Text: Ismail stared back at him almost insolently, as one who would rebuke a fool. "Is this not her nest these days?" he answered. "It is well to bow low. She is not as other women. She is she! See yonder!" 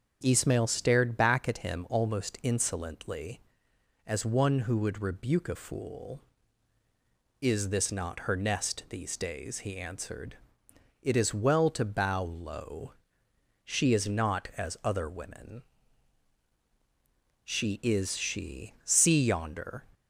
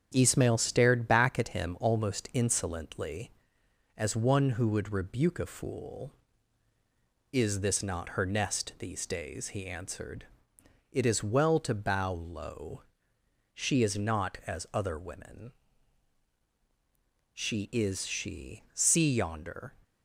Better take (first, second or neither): first